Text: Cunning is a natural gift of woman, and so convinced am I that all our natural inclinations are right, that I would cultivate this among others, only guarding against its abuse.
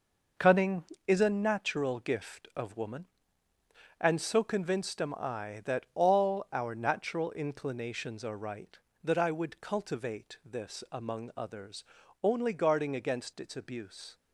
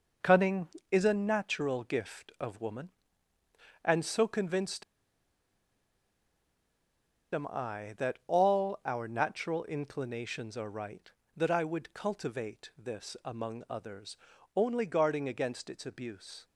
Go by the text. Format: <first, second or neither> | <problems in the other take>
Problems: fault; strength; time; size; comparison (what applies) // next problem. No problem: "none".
first | pauses between "convinced" and "am"; strong; at 4.8 s; 2.5 s long